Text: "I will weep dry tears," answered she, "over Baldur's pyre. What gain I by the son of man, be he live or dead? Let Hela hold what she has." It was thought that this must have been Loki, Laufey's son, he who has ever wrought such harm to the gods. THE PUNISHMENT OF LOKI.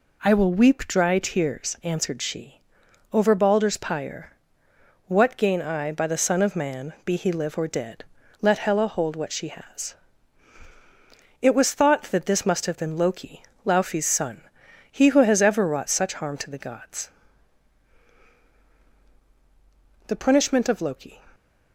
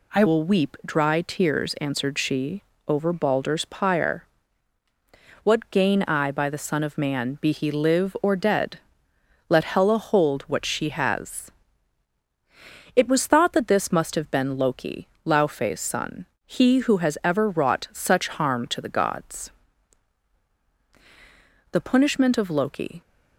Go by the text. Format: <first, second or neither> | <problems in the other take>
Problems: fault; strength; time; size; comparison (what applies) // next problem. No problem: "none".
first | changes voice at "will"; from 0.2 s on; 22.8 s long